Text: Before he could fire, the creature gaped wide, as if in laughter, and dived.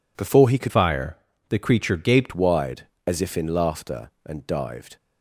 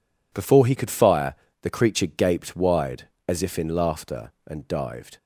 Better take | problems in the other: second | changes voice from "fire" to "gaped"; from 0.6 to 2.3 s; 1.7 s long

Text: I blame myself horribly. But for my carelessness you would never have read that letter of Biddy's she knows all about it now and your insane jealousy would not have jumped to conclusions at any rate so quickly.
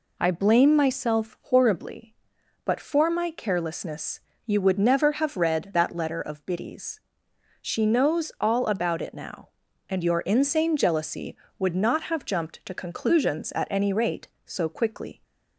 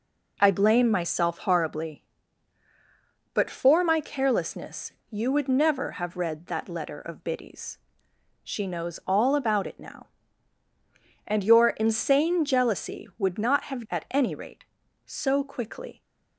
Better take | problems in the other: first | pauses between "carelessness" and "you"; slight; at 4.9 s; 0.18 s long; slight in the first // pauses between "Biddy's" and "she"; noticeable; at 7.7 s; 0.70 s long; noticeable in the first // skips "jumped to conclusions"; at 13.8 s

